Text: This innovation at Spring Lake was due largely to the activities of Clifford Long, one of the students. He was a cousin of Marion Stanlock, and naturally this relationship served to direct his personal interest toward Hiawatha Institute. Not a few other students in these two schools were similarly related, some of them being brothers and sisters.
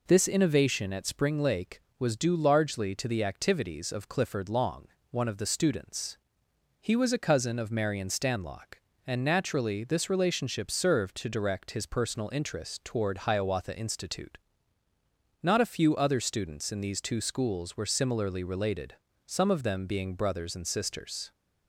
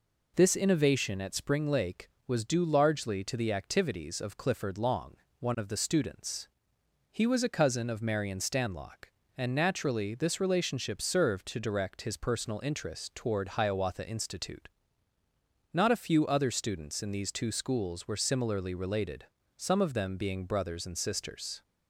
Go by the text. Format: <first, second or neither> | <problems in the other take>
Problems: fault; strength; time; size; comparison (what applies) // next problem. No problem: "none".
neither | none